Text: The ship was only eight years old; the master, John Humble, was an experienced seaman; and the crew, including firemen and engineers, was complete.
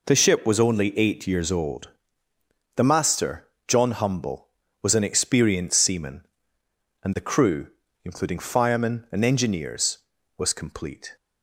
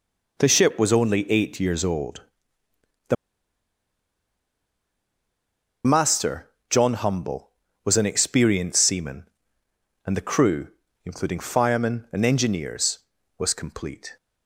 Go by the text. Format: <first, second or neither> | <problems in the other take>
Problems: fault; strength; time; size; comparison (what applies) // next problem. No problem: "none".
first | pauses between "the" and "master"; strong; at 3.1 s; 2.7 s long